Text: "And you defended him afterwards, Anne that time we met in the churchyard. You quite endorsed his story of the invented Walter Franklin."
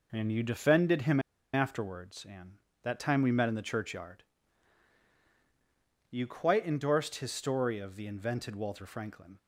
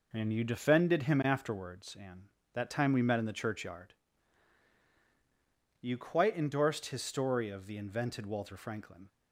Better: second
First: pauses between "him" and "afterwards"; slight; at 1.1 s; 0.33 s long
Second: none

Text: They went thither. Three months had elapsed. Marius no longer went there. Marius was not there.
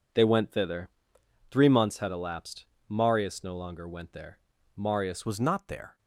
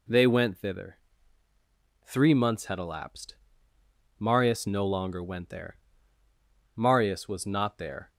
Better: second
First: changes voice at "was"; from 5.2 s on; 0.7 s long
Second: none

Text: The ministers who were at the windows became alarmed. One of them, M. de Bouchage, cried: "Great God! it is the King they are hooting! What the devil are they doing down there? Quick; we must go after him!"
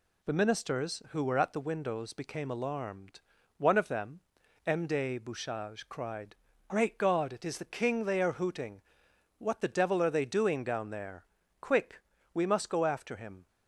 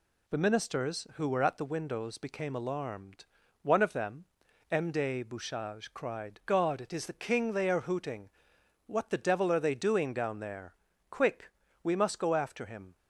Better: first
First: none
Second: skips "Great"; at 6.4 s

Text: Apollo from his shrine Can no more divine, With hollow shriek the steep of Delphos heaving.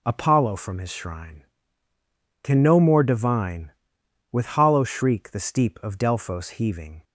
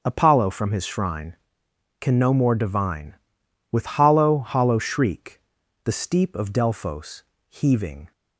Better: first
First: none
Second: starts louder than the rest; until 1.0 s; 6 dB // says "hollow" twice; at 4.3 s // pauses between "shriek" and "the"; noticeable; at 5.3 s; 0.46 s long // pauses between "Delphos" and "heaving"; slight; at 7.2 s; 0.26 s long

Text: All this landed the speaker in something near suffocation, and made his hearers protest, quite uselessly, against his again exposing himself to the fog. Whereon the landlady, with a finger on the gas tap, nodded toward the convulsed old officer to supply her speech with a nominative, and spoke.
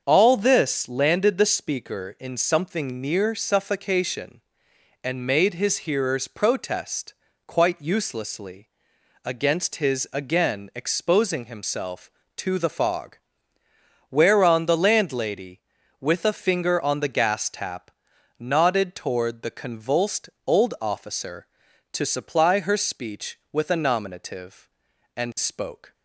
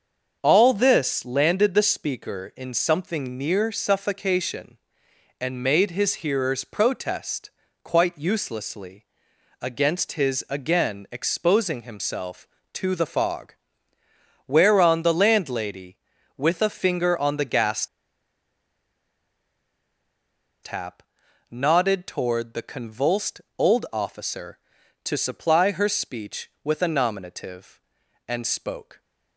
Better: first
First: starts louder than the rest; until 1.0 s; 6.5 dB // pauses between "convulsed" and "old"; slight; at 20.2 s; 0.16 s long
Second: starts louder than the rest; until 1.4 s; 6.5 dB // pauses between "gas" and "tap"; strong; at 17.8 s; 2.7 s long // pauses between "convulsed" and "old"; slight; at 23.4 s; 0.16 s long

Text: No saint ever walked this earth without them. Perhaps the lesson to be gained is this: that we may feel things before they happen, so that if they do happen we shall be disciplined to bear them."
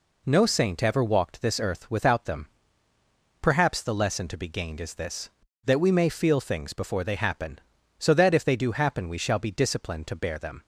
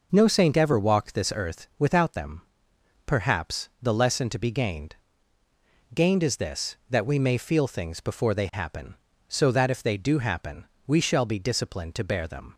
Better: first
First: none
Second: says "gained" twice; at 5.9 s // pauses between "happen" and "we"; slight; at 10.6 s; 0.20 s long

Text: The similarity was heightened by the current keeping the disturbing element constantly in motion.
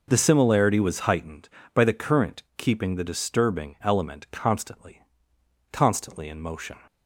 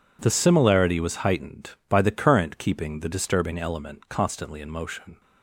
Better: second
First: pauses between "current" and "keeping"; slight; at 2.4 s; 0.16 s long // says "constantly" twice; at 5.7 s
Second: none

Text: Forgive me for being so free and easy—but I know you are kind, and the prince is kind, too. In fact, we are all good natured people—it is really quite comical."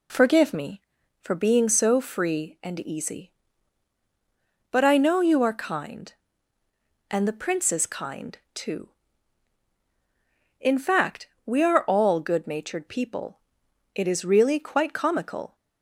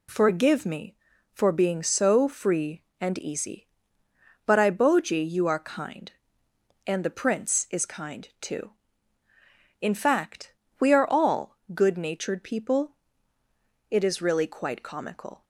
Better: first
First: none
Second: says "boji" for "know"; at 4.7 s // pauses between "all" and "good"; slight; at 11.5 s; 0.18 s long

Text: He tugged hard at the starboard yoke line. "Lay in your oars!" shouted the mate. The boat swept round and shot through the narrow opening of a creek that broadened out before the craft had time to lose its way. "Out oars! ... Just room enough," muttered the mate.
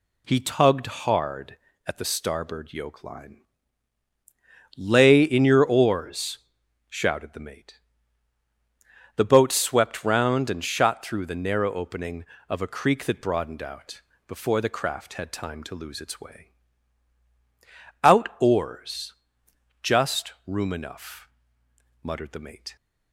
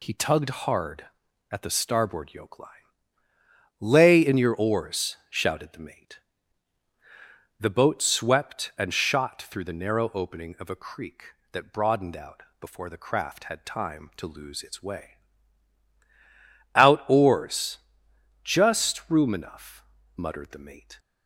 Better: first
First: pauses between "out" and "before"; slight; at 14.0 s; 0.24 s long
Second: skips "round"; at 8.7 s // pauses between "out" and "before"; slight; at 12.4 s; 0.16 s long

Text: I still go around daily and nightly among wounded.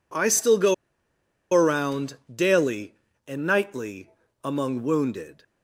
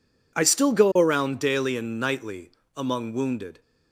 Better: second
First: pauses between "go" and "around"; noticeable; at 0.7 s; 0.78 s long // pauses between "around" and "daily"; slight; at 2.1 s; 0.18 s long // pauses between "nightly" and "among"; slight; at 4.0 s; 0.34 s long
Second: pauses between "nightly" and "among"; slight; at 2.5 s; 0.26 s long

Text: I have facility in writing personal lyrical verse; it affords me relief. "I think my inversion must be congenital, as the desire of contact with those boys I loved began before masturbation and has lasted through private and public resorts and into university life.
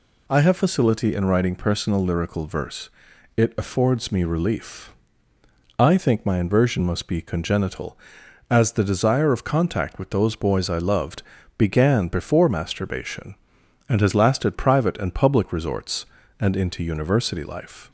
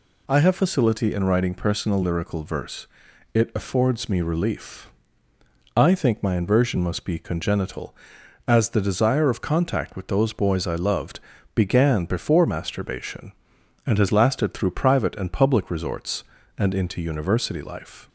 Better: second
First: pauses between "loved" and "began"; at 11.2 s; 0.38 s long // skips "through"; at 14.5 s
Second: pauses between "loved" and "began"; at 11.1 s; 0.38 s long

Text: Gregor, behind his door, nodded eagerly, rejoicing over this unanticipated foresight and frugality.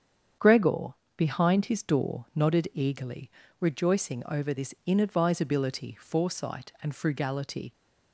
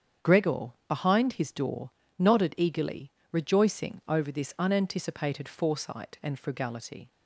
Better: second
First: starts louder than the rest; strong; until 1.6 s; 8 dB // says "inadvisability" for "unanticipated"; at 4.8 s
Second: starts louder than the rest; strong; until 1.3 s; 8 dB

